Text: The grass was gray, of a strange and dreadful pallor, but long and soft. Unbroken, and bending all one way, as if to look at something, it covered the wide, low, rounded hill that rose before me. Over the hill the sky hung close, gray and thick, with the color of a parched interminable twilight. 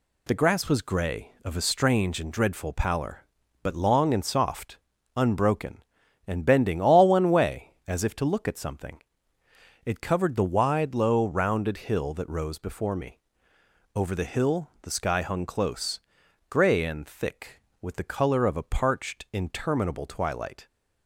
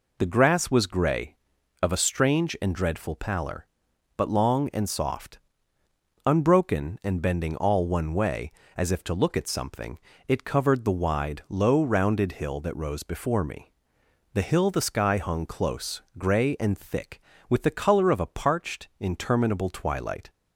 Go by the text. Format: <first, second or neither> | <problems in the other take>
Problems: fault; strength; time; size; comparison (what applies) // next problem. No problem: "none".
first | skips "Over"; at 14.0 s